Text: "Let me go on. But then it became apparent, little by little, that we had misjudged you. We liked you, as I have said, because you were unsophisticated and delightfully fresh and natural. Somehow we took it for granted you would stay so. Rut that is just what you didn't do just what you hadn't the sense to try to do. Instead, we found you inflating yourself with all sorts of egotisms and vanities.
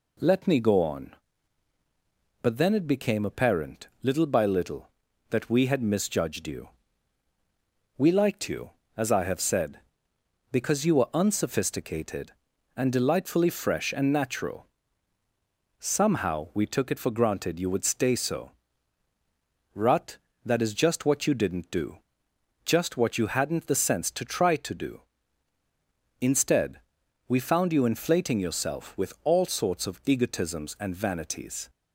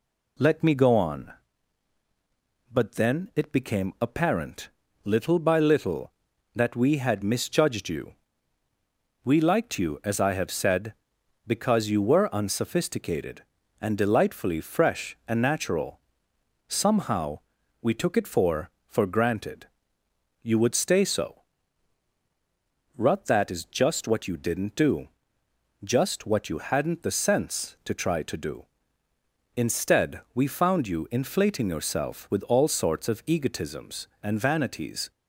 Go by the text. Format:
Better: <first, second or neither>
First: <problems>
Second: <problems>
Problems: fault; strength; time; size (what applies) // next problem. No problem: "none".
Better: first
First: pauses between "do" and "just"; noticeable; at 21.9 s; 0.66 s long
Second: pauses between "Somehow" and "we"; at 17.3 s; 0.40 s long // says "for" twice; at 18.8 s // pauses between "granted" and "you"; noticeable; at 19.6 s; 0.76 s long // pauses between "do" and "just"; noticeable; at 25.0 s; 0.74 s long